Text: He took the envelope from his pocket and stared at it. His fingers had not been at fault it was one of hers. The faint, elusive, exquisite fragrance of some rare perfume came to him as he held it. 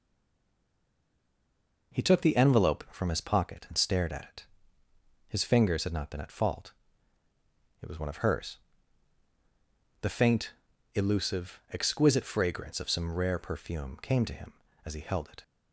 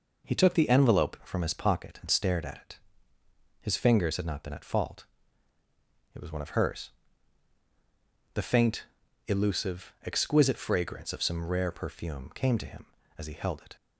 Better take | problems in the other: second | stays silent before the first word; noticeable; until 1.9 s; 1.9 s long // pauses between "fault" and "it"; at 6.7 s; 1.1 s long; also in the second

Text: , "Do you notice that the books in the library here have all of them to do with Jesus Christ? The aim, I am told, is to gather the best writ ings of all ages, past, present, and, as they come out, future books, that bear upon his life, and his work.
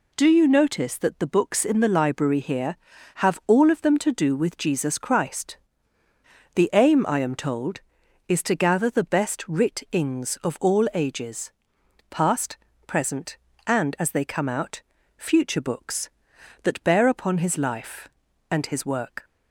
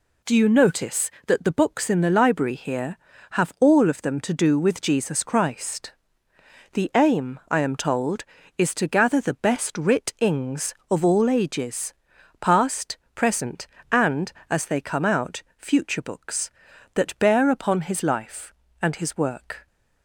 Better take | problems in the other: neither | none

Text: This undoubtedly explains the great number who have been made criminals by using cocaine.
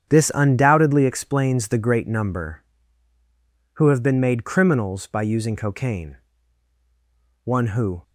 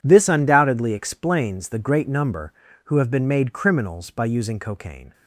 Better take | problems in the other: second | starts louder than the rest; strong; until 1.1 s; 8.5 dB // goes on to say "One who"; from 7.4 s on; 0.58 s long

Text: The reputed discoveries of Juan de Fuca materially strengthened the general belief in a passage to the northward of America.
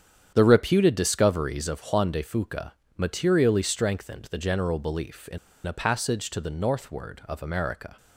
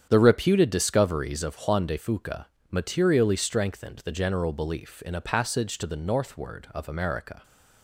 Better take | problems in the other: second | starts louder than the rest; strong; until 1.3 s; 8.5 dB; strong in the second // pauses between "Fuca" and "materially"; slight; at 2.7 s; 0.26 s long; slight in the second // pauses between "in" and "a"; slight; at 5.3 s; 0.28 s long

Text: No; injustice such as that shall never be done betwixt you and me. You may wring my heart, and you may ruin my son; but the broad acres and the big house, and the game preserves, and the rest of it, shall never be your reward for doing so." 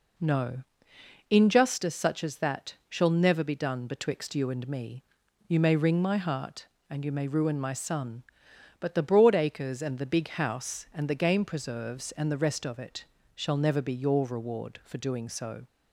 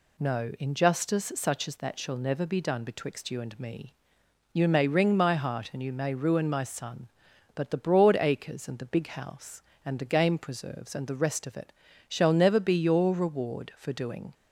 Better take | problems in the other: first | stops before "so"; at 14.3 s

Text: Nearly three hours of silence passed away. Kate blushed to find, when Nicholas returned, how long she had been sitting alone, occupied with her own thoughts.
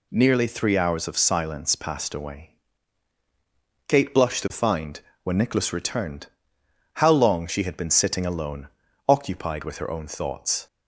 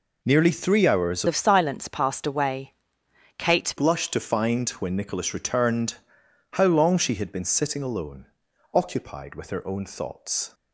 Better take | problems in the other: first | changes voice from "of" to "Kate"; from 1.2 to 3.7 s; 2.5 s long

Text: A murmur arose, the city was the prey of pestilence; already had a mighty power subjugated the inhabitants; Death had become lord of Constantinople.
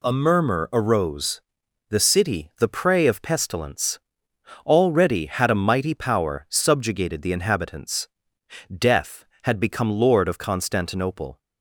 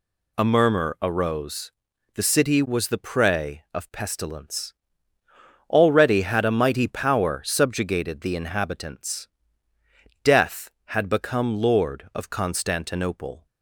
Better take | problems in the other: second | skips "was"; at 2.5 s

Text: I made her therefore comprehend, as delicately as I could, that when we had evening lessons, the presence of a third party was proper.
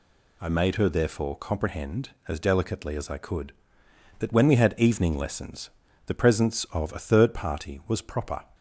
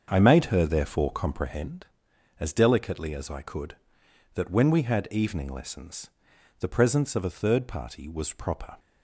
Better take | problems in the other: first | starts louder than the rest; until 1.7 s; 6.5 dB

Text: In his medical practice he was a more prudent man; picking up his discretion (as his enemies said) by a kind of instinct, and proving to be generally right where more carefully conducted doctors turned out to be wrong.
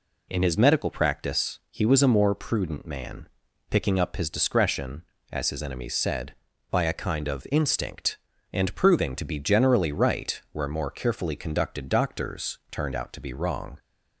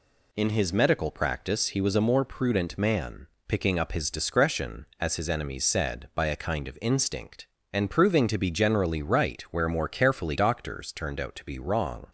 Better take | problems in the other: first | skips "conducted"; at 10.3 s

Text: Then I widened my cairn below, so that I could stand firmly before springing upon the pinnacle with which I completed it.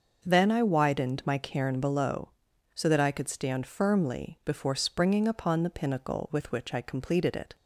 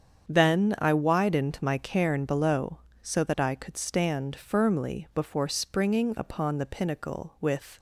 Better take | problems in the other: first | starts louder than the rest; strong; until 1.3 s; 7.5 dB; noticeable in the first // stops before "which I completed it"; at 7.7 s

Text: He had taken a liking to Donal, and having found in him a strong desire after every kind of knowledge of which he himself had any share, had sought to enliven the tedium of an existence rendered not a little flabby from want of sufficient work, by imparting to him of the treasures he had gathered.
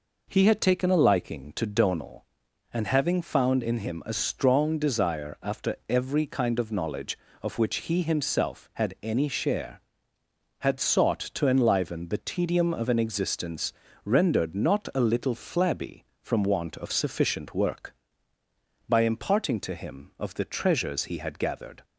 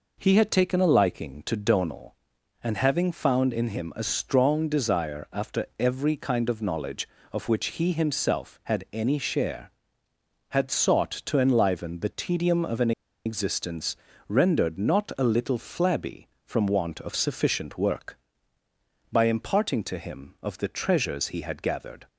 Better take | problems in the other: first | pauses between "an" and "existence"; slight; at 12.9 s; 0.34 s long // pauses between "existence" and "rendered"; slight; at 13.9 s; 0.32 s long; slight in the first

